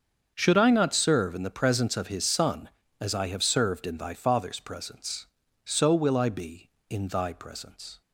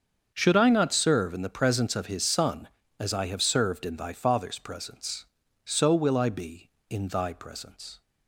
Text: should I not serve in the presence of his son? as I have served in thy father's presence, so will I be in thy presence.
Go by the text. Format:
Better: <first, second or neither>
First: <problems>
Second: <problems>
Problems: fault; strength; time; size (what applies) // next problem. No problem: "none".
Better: neither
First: starts louder than the rest; strong; until 1.3 s; 7 dB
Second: starts louder than the rest; strong; until 1.3 s; 7 dB